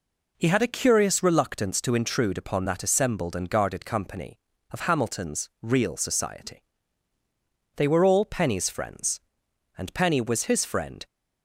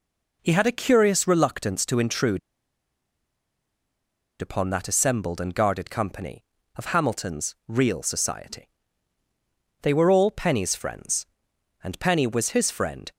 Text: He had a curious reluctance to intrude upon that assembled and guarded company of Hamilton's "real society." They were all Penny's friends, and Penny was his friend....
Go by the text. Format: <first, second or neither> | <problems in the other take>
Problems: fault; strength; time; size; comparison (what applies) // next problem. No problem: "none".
first | pauses between "intrude" and "upon"; strong; at 2.3 s; 2.0 s long